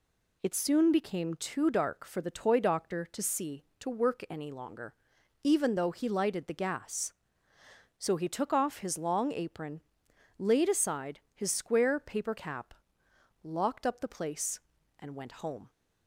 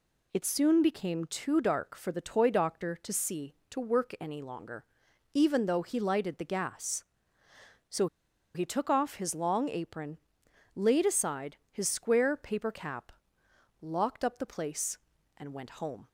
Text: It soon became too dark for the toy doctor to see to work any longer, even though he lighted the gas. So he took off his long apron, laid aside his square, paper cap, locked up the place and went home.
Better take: first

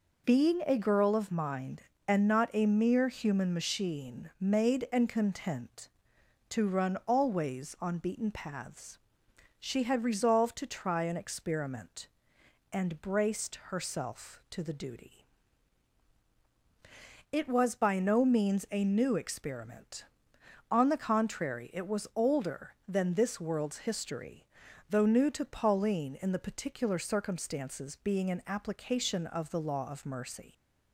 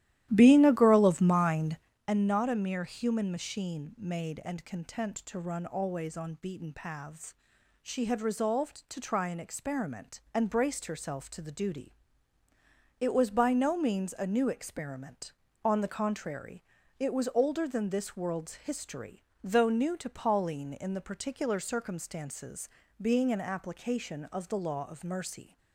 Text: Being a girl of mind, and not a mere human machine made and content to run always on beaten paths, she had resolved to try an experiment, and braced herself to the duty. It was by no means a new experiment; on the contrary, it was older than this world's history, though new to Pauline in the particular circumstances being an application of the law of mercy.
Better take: first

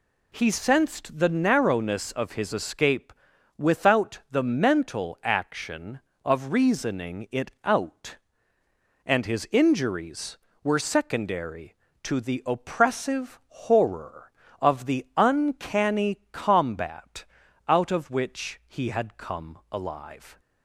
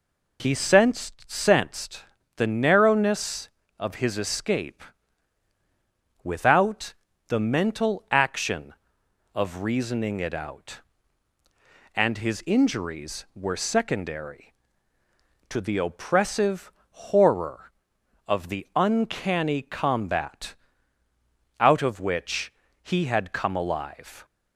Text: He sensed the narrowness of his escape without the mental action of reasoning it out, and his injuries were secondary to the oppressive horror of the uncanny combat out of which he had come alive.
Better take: first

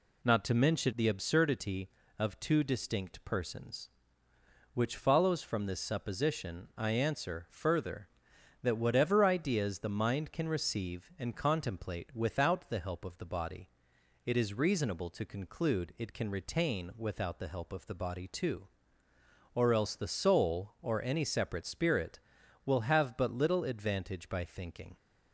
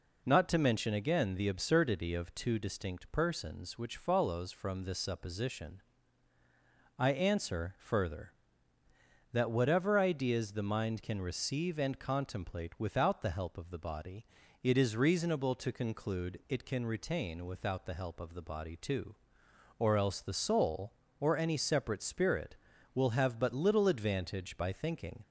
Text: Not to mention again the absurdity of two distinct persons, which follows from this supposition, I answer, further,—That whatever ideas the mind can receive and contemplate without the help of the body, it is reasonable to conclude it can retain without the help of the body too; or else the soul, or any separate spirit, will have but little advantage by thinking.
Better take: second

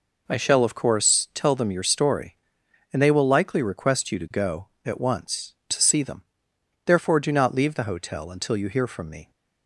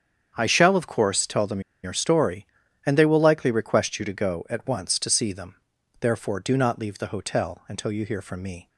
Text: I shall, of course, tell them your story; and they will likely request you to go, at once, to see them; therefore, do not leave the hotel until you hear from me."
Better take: first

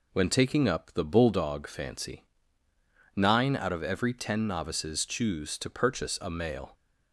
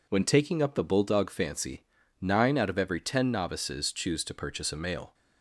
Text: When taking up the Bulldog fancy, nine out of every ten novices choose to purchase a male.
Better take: neither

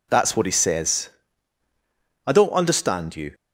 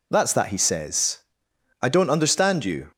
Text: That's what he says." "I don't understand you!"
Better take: first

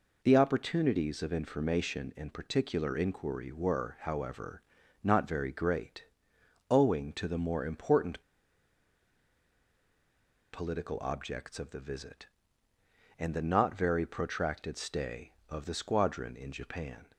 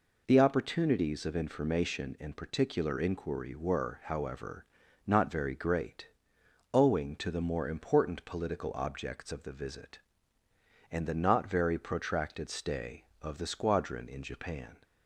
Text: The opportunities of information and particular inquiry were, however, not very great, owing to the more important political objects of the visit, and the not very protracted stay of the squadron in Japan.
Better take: second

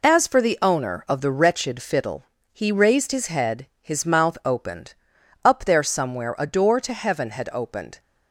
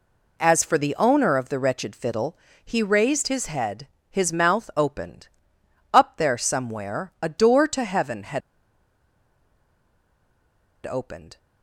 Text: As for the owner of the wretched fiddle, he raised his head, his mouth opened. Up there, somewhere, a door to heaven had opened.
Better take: first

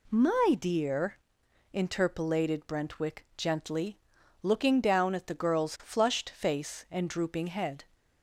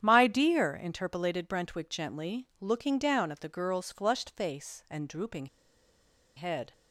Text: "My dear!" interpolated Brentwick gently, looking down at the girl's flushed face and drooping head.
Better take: first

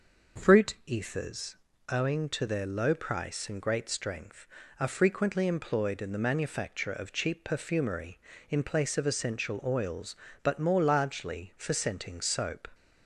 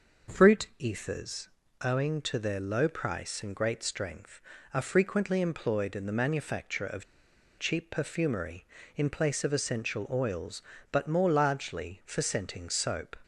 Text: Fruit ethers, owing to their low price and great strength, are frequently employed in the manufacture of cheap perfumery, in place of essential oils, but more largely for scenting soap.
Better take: first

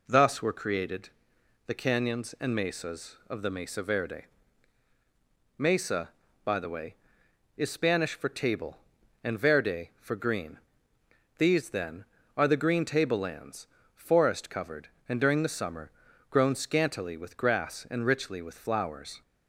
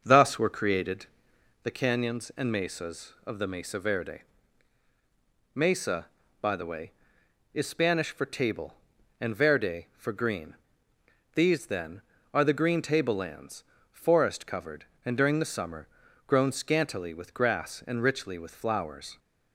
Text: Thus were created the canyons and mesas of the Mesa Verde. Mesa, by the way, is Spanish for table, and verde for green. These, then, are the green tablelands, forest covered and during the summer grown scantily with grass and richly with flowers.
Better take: first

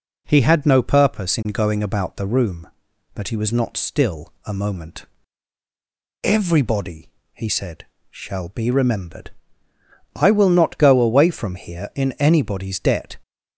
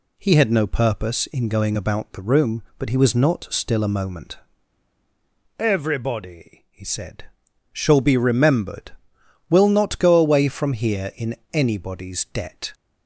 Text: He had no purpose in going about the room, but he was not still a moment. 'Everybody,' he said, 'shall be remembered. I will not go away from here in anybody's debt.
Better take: first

